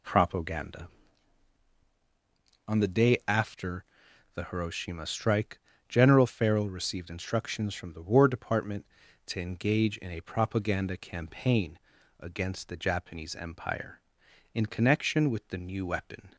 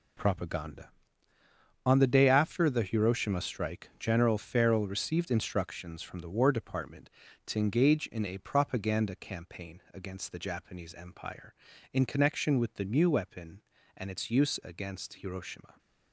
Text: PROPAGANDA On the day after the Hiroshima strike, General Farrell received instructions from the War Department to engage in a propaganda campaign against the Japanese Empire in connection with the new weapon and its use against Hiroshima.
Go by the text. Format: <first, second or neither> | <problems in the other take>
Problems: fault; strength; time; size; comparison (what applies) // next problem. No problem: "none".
second | pauses between "after" and "the"; noticeable; at 3.8 s; 0.52 s long // pauses between "campaign" and "against"; at 11.7 s; 0.40 s long // stops before "and its use against Hiroshima"; at 16.3 s